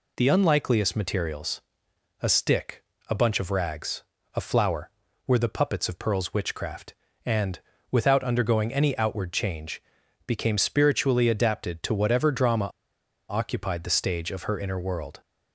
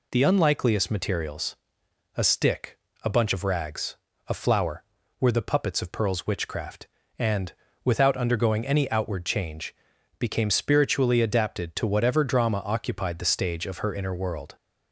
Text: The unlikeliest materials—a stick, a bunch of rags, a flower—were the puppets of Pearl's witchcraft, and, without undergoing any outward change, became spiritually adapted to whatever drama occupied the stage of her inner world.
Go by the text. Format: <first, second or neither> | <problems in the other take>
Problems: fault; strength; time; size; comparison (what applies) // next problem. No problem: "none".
second | pauses between "drama" and "occupied"; noticeable; at 12.6 s; 0.61 s long